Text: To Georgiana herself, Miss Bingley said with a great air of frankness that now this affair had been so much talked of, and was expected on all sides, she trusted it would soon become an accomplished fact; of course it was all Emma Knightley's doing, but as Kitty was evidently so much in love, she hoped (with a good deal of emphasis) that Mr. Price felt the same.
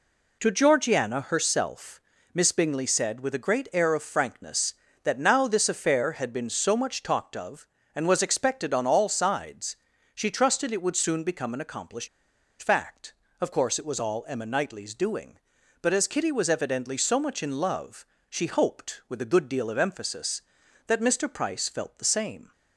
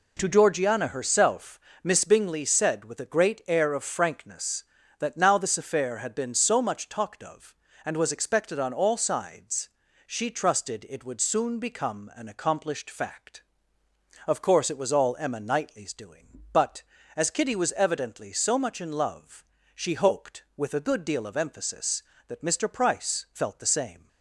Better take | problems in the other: second | pauses between "accomplished" and "fact"; noticeable; at 12.0 s; 0.53 s long

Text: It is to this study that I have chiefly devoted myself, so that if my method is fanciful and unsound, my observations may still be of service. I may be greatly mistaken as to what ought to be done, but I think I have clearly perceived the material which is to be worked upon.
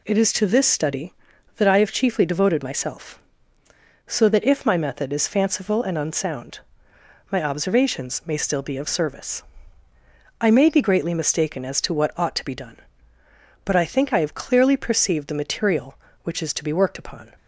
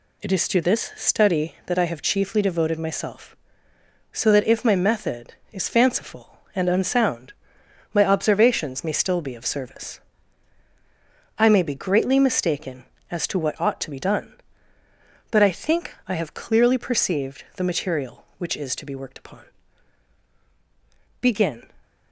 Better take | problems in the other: first | goes on to say "Begin"; slight; from 21.2 s on; 0.48 s long

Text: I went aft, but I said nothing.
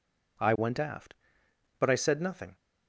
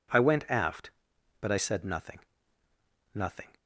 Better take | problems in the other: first | says "nothing" twice; at 3.1 s

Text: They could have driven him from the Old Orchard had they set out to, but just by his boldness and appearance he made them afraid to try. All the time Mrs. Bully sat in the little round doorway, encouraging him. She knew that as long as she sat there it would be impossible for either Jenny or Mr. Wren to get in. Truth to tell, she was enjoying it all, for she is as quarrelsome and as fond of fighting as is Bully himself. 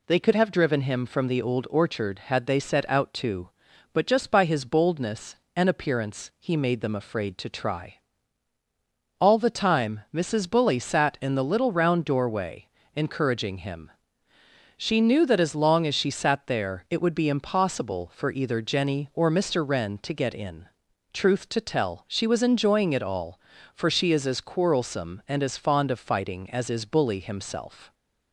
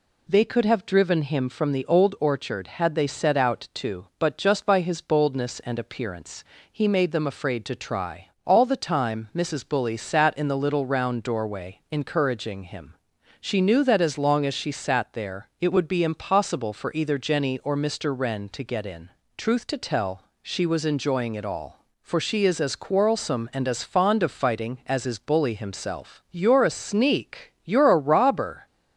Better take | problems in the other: first | pauses between "appearance" and "he"; slight; at 6.4 s; 0.26 s long // goes on to say "You're a sneak You're a robber"; strong; from 26.2 s on; 2.3 s long

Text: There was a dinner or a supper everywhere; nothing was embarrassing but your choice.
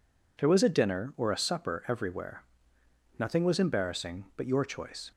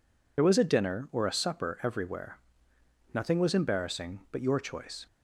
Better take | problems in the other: first | loses the start of "There"; at 0.3 s; 40 ms

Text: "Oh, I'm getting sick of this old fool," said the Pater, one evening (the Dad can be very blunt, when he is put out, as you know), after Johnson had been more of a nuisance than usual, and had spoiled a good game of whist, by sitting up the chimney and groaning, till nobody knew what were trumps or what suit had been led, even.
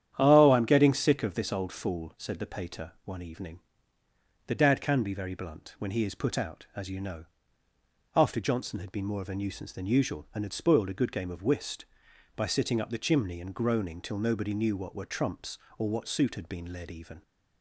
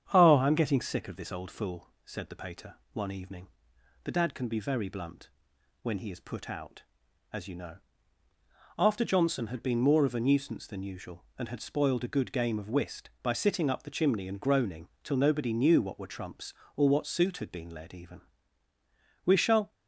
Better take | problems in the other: first | starts louder than the rest; strong; until 1.1 s; 8.5 dB; strong in the first // goes on to say "We shall"; slight; from 19.2 s on; 0.48 s long

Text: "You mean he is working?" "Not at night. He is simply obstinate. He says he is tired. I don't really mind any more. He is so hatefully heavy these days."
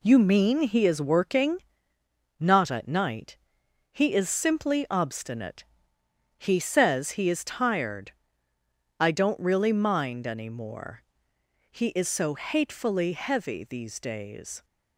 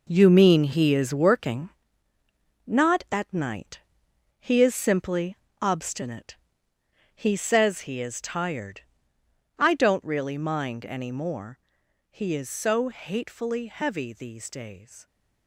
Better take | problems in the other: first | gets quieter; strong; throughout; 10.5 dB // pauses between "simply" and "obstinate"; slight; at 5.3 s; 0.24 s long

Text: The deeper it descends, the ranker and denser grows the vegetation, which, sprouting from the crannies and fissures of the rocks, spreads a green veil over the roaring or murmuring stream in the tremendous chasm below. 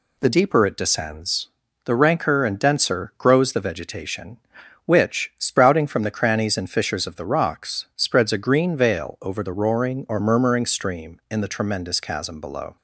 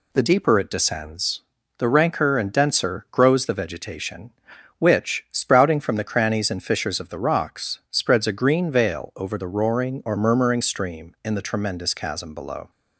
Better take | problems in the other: neither | none

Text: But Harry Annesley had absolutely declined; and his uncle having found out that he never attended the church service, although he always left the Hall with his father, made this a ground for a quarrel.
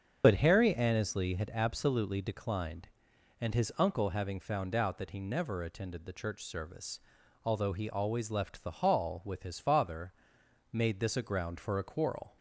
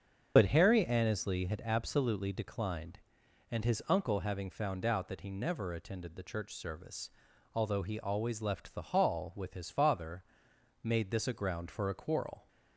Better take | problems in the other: neither | starts louder than the rest; the same in both

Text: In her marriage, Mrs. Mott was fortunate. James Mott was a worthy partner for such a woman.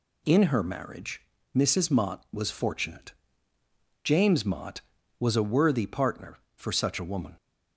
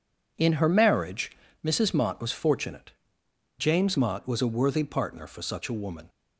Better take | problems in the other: neither | none

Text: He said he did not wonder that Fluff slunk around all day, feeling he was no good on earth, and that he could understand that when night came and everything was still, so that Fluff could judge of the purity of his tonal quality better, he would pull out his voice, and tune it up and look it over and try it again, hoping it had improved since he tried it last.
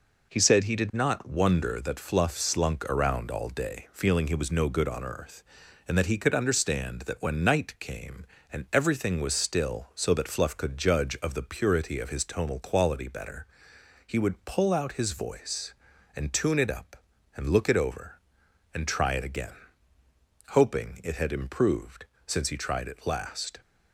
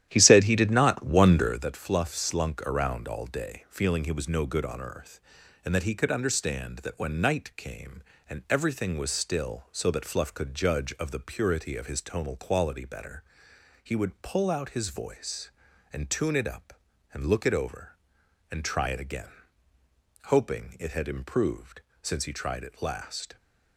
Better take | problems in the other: first | starts louder than the rest; strong; until 1.7 s; 11.5 dB // pauses between "improved" and "since"; slight; at 21.8 s; 0.22 s long; slight in the first

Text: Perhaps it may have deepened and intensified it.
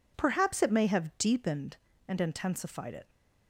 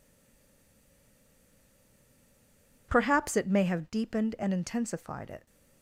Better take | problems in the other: first | stays silent before the first word; strong; until 2.8 s; 2.8 s long

